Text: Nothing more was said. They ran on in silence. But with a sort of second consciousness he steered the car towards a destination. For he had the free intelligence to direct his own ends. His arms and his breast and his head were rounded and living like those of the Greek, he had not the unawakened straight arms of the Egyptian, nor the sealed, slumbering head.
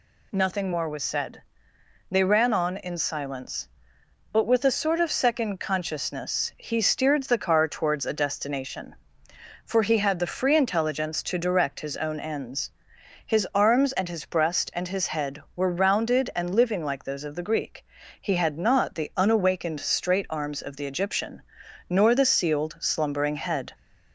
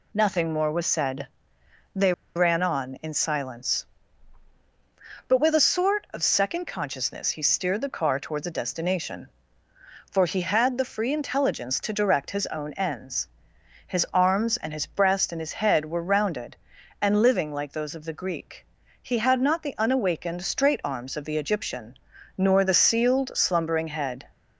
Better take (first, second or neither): first